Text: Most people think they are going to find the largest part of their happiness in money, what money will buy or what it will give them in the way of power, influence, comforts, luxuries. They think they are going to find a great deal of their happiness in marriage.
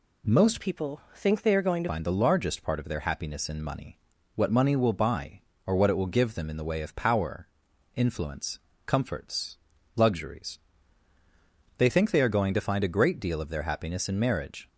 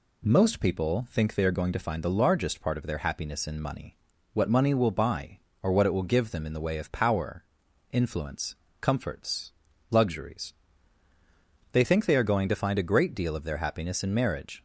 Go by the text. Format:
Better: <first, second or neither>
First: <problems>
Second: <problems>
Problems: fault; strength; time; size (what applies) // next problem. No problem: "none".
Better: second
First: changes voice from "people" to "to"; from 0.5 to 1.8 s; 1.3 s long // pauses between "people" and "think"; slight; at 0.9 s; 0.16 s long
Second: none